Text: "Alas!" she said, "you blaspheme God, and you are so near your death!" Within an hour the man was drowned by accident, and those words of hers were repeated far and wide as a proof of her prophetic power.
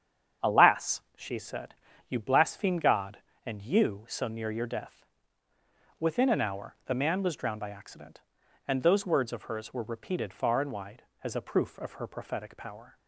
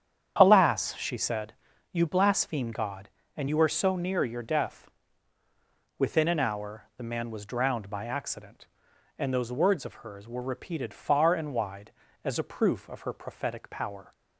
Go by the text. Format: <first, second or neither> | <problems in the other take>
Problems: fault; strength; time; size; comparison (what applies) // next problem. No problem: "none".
second | starts louder than the rest; strong; until 1.5 s; 8 dB; strong in the second // skips "are"; at 4.0 s